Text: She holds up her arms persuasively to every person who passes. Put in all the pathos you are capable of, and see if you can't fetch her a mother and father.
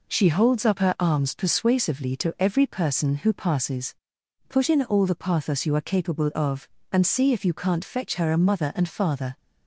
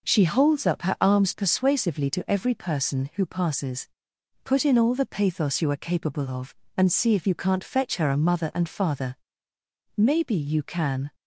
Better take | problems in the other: first | goes on to say "Maybe you can"; noticeable; from 9.9 s on; 1.1 s long

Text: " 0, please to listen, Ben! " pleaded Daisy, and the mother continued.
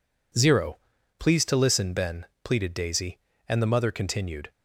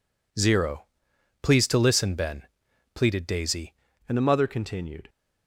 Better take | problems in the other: first | changes voice at "and"; from 4.0 s on; 1.0 s long

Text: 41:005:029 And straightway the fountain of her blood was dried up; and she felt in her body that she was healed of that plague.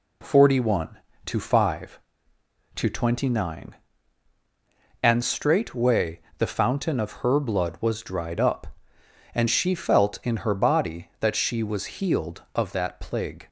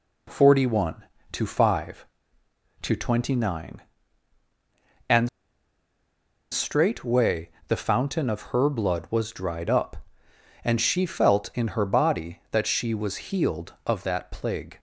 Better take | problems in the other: first | pauses between "And" and "straightway"; at 5.2 s; 1.2 s long // pauses between "straightway" and "the"; slight; at 7.5 s; 0.16 s long; slight in the first

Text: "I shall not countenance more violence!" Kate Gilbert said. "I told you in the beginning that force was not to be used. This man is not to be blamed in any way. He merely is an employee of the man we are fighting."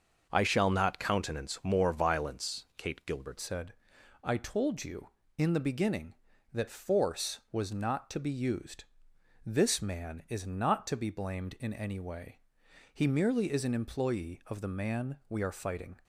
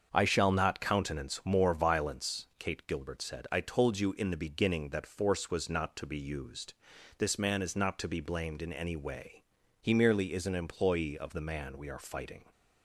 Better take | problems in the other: second | starts louder than the rest; until 1.3 s; 6.5 dB; also in the second // changes voice at "said"; from 3.3 s on; 12.6 s long

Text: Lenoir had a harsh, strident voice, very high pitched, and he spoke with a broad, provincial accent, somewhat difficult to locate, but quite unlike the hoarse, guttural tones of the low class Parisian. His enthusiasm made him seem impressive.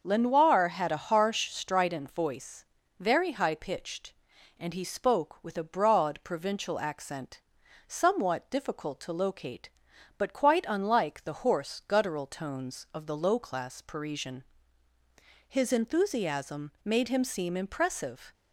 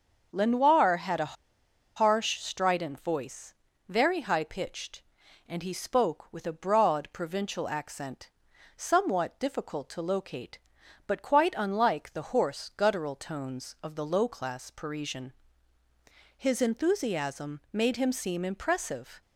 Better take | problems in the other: first | starts louder than the rest; until 1.3 s; 6 dB; also in the first // pauses between "a" and "harsh"; noticeable; at 1.3 s; 0.61 s long

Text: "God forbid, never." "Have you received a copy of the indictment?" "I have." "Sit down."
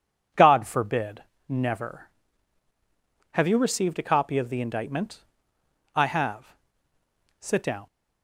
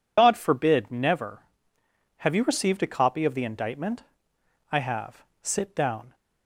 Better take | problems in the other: first | loses the start of "God"; at 0.1 s; 70 ms

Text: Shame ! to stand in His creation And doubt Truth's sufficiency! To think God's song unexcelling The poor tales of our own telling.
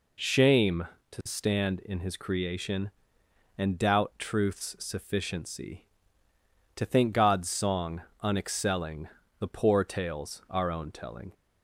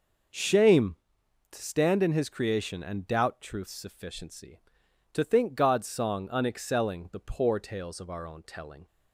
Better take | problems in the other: second | pauses between "song" and "unexcelling"; slight; at 8.0 s; 0.20 s long // pauses between "unexcelling" and "The"; slight; at 9.0 s; 0.34 s long // skips "of"; at 10.4 s

